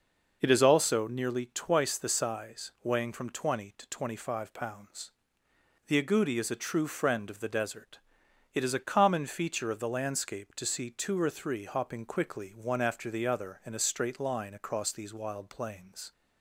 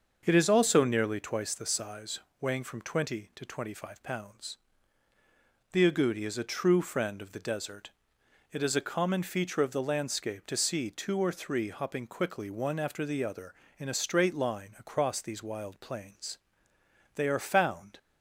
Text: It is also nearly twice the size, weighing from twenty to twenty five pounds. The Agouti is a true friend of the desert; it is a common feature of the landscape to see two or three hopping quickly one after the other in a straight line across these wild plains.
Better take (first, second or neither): first